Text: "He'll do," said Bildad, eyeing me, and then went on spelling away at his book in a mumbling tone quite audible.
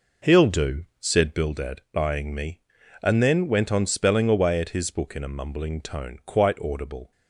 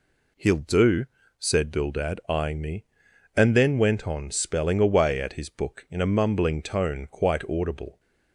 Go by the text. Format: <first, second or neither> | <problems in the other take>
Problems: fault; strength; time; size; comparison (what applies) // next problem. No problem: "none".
second | starts louder than the rest; noticeable; until 1.6 s; 4.5 dB